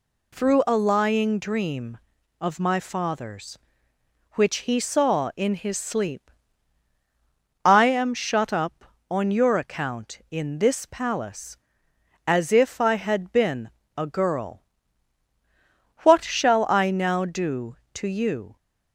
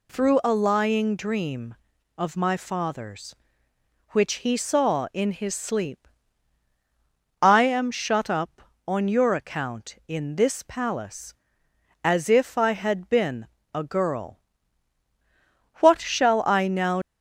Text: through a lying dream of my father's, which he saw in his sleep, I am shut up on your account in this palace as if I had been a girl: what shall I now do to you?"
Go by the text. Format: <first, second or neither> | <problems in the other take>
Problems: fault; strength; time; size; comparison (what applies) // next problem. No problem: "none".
first | pauses between "been" and "a"; slight; at 13.4 s; 0.26 s long; slight in the first // stops before "do to you"; at 17.0 s